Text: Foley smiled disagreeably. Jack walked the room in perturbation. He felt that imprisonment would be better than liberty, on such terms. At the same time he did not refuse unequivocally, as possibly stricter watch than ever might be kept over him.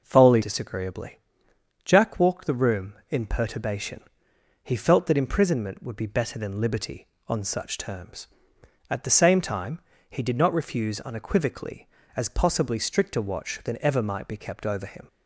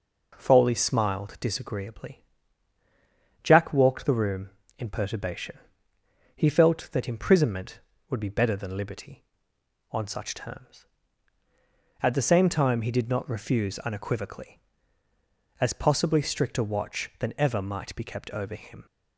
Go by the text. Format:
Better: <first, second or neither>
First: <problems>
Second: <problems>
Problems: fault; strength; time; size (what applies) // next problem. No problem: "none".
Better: second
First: skips "smiled"; at 0.4 s // pauses between "time" and "he"; slight; at 9.8 s; 0.26 s long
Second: none